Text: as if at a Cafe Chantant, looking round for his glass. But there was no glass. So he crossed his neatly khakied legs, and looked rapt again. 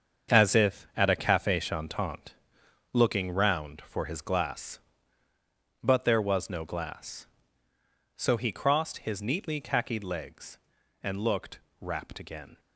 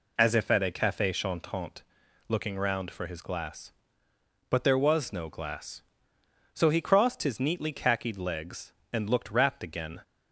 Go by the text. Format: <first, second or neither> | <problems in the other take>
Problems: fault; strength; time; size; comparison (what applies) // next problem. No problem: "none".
second | gets quieter; strong; throughout; 10 dB // pauses between "looked" and "rapt"; slight; at 11.5 s; 0.20 s long